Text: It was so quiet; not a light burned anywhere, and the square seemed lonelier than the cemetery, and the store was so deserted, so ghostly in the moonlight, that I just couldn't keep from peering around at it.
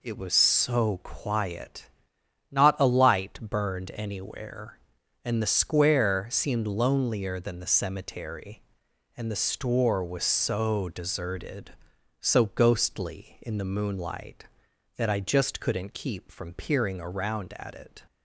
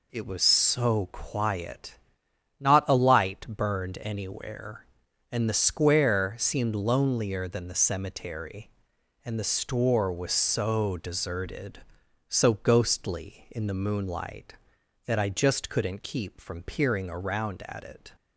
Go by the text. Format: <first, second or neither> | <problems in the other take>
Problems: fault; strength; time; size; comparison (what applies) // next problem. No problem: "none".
neither | none